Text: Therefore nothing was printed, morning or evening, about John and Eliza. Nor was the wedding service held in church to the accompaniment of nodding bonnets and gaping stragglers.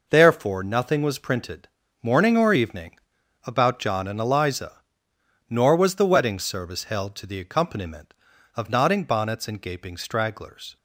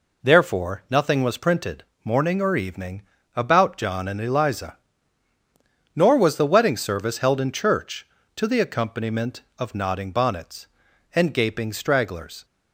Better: second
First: skips "in church"; at 7.1 s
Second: none

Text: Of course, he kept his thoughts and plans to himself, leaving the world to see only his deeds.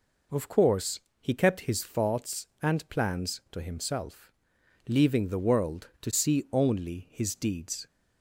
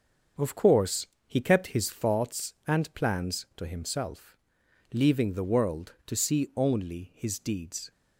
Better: first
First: none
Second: gets quieter; noticeable; throughout; 5.5 dB

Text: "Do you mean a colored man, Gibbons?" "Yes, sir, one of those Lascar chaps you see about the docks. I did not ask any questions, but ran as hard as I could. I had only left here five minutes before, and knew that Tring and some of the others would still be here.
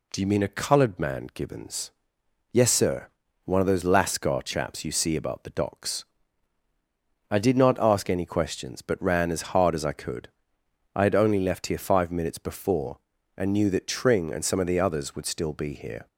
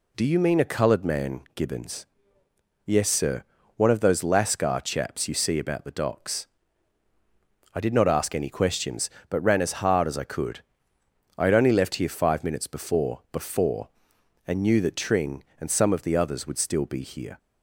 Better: first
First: none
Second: says "before" twice; at 13.3 s

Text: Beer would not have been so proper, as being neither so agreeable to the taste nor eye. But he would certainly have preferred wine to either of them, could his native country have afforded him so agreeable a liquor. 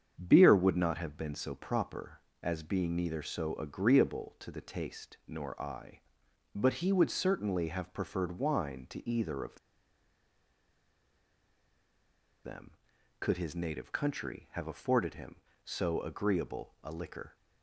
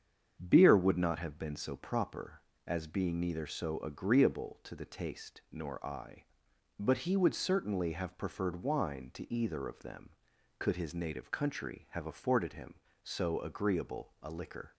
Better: second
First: starts louder than the rest; strong; until 1.2 s; 7.5 dB // pauses between "of" and "them"; strong; at 9.5 s; 2.8 s long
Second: starts louder than the rest; strong; until 1.4 s; 7.5 dB

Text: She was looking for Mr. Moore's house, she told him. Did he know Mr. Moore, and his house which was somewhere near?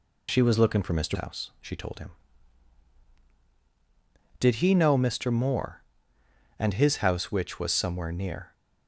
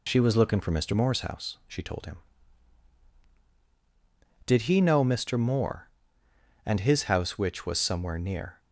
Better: second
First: skips "Moore's"; at 1.1 s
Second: none

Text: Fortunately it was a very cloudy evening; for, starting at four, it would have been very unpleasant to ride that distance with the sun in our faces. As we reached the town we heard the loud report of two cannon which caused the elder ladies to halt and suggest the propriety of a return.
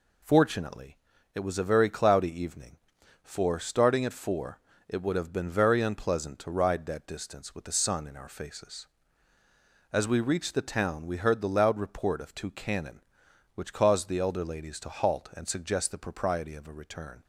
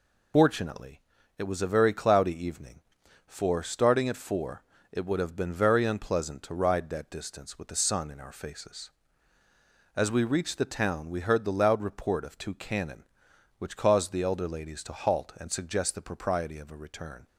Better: first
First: pauses between "Fortunately" and "it"; at 0.9 s; 0.40 s long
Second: loses the start of "Fortunately"; at 0.3 s; 75 ms // pauses between "Fortunately" and "it"; at 0.9 s; 0.40 s long

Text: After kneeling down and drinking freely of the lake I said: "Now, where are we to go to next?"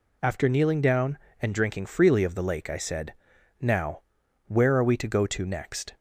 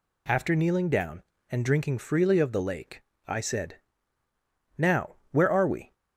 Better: first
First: none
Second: pauses between "lake" and "I"; slight; at 3.0 s; 0.28 s long // stops before "to go to next"; at 5.9 s

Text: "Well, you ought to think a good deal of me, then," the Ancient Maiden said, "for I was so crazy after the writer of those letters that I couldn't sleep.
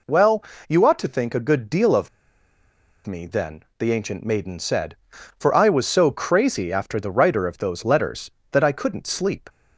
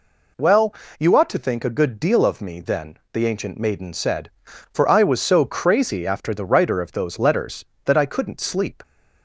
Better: second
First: pauses between "of" and "me"; at 2.0 s; 0.98 s long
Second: none

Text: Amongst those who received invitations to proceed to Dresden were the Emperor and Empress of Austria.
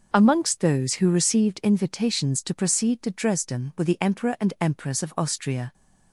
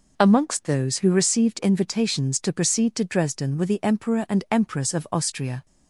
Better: neither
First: none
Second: none

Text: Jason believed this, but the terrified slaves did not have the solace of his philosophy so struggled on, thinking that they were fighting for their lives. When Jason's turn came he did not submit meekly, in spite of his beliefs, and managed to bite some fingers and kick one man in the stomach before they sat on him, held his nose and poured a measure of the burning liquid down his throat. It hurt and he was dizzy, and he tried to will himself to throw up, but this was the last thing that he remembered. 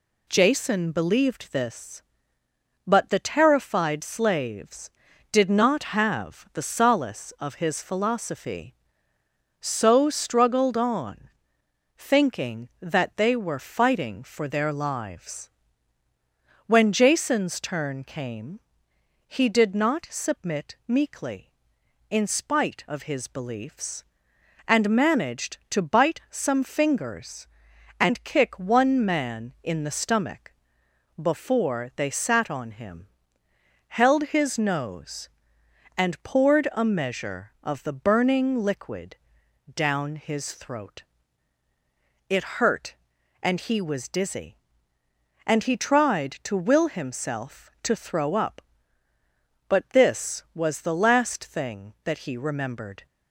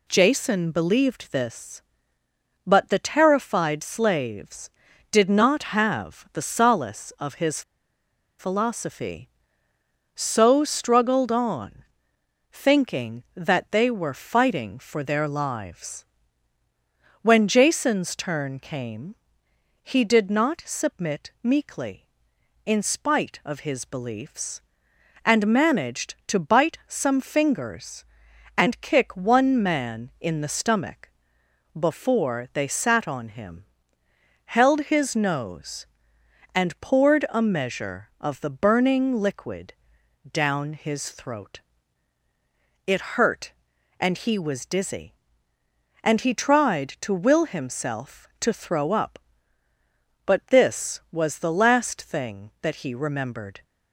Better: first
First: pauses between "came" and "he"; noticeable; at 18.5 s; 0.70 s long // pauses between "stomach" and "before"; noticeable; at 30.5 s; 0.68 s long // pauses between "liquid" and "down"; noticeable; at 39.1 s; 0.58 s long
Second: pauses between "his" and "philosophy"; noticeable; at 7.6 s; 0.77 s long // pauses between "came" and "he"; noticeable; at 19.1 s; 0.70 s long // pauses between "stomach" and "before"; noticeable; at 31.0 s; 0.68 s long // pauses between "liquid" and "down"; noticeable; at 39.7 s; 0.58 s long

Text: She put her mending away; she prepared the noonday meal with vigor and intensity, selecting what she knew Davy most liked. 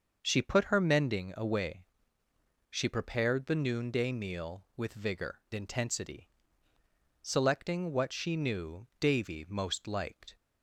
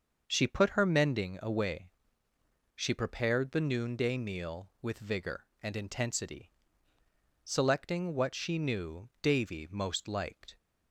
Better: second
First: starts louder than the rest; until 1.2 s; 6.5 dB // skips "and"; at 5.4 s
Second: starts louder than the rest; until 1.2 s; 6.5 dB

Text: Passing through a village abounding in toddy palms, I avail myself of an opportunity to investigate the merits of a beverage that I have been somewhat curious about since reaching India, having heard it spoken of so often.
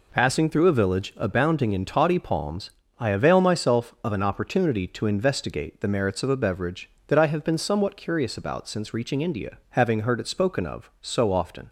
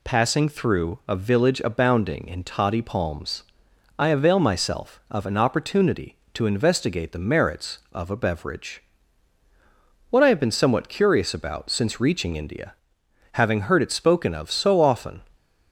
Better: first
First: none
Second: says "what" for "that"; at 10.0 s

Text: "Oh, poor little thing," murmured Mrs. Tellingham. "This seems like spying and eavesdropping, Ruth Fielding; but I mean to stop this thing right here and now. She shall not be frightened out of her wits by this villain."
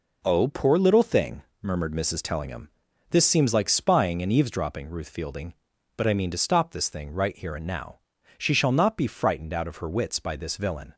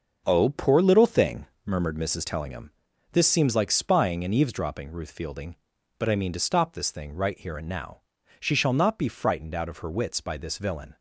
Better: first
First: none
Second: starts louder than the rest; noticeable; until 2.0 s; 6 dB

